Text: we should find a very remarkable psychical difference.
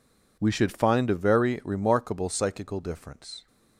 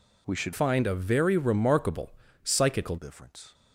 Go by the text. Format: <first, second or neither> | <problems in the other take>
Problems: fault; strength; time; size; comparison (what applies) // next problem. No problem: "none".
first | changes voice from "find" to "psychical"; from 0.5 to 2.9 s; 2.4 s long // pauses between "remarkable" and "psychical"; slight; at 2.1 s; 0.32 s long